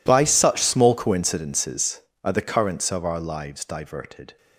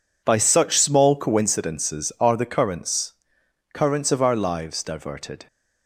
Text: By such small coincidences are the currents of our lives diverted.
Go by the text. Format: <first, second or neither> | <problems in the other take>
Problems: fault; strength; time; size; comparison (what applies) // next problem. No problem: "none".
first | says "currents" twice; at 3.7 s